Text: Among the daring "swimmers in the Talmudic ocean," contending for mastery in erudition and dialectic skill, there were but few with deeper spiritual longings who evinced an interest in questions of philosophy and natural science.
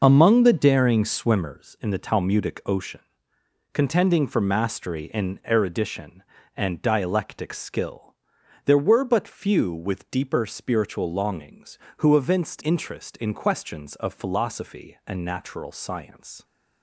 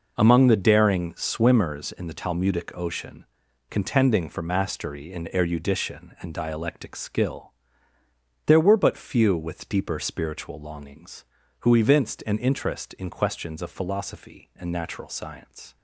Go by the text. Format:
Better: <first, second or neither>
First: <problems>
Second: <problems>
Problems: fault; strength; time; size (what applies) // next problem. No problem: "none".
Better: second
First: skips "an"; at 12.6 s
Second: none